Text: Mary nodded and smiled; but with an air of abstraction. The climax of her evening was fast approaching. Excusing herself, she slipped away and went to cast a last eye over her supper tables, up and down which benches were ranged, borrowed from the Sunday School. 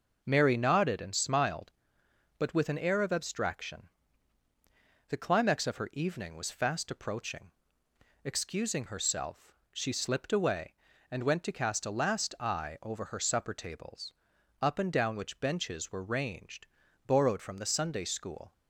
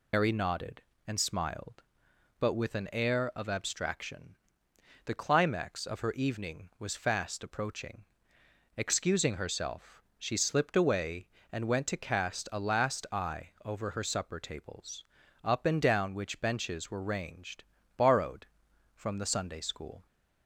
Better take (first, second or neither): first